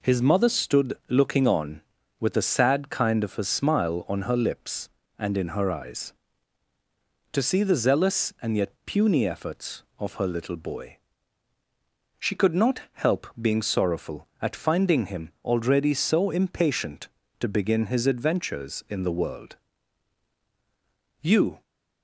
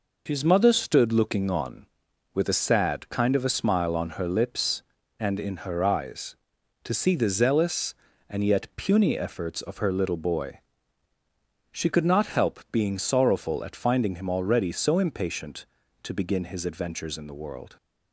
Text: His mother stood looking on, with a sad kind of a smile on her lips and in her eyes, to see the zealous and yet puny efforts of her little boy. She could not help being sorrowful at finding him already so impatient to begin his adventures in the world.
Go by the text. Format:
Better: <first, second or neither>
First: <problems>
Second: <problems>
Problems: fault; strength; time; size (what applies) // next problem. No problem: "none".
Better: second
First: goes on to say "You"; slight; from 21.2 s on; 0.40 s long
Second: none